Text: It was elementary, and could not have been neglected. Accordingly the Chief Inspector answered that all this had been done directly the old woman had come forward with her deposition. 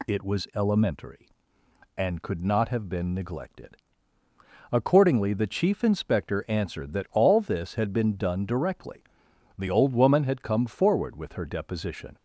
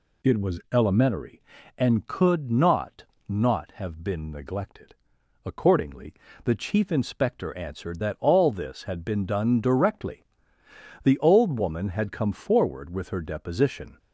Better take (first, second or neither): first